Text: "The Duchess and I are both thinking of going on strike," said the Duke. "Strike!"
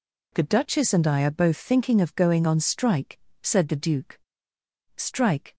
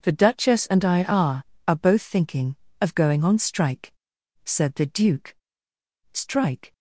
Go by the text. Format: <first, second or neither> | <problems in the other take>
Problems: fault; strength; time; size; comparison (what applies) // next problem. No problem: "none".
first | says "are" twice; at 1.6 s